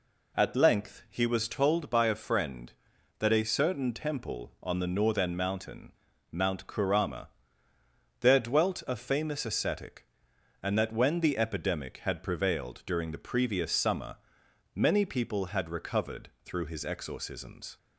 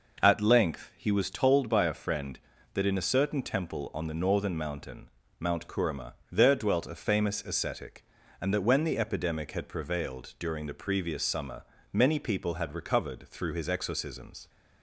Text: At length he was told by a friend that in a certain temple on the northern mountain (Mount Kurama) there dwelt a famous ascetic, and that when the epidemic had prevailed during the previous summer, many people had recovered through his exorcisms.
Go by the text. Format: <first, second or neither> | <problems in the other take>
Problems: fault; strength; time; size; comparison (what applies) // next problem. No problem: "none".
second | skips "in"; at 3.3 s // pauses between "recovered" and "through"; slight; at 16.2 s; 0.16 s long